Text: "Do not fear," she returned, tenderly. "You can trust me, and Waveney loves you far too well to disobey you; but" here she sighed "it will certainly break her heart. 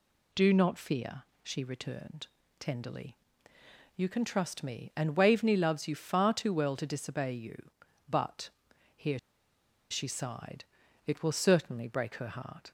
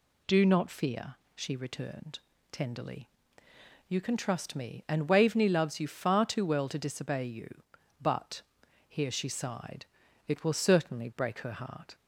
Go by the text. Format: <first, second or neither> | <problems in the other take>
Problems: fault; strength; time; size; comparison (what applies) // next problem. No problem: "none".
second | pauses between "but" and "here"; noticeable; at 8.4 s; 0.48 s long; noticeable in the second // pauses between "here" and "she"; noticeable; at 9.1 s; 0.72 s long // pauses between "sighed" and "it"; at 10.6 s; 0.42 s long; also in the second